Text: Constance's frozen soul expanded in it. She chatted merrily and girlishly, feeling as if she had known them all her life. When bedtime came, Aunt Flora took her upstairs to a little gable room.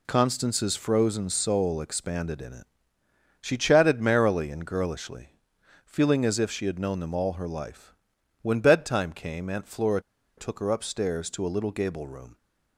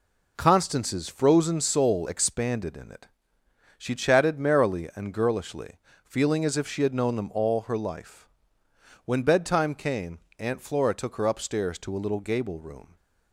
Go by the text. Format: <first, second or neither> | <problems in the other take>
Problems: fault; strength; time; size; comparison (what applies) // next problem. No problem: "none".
second | pauses between "Flora" and "took"; at 9.9 s; 0.37 s long